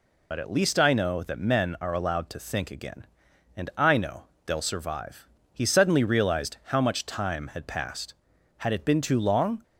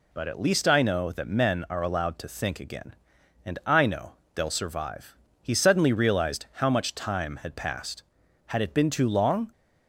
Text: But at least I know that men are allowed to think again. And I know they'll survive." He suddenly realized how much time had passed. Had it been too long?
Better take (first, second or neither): second